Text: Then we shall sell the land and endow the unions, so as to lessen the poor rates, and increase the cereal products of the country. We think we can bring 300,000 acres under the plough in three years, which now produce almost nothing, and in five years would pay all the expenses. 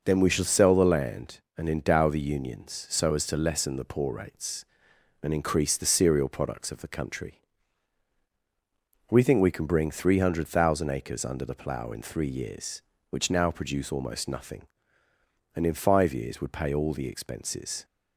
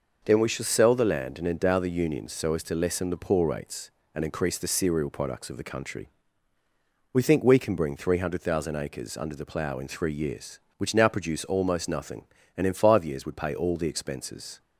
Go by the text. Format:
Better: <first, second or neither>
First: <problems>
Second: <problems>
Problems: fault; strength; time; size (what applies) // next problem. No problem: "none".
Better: neither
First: none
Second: none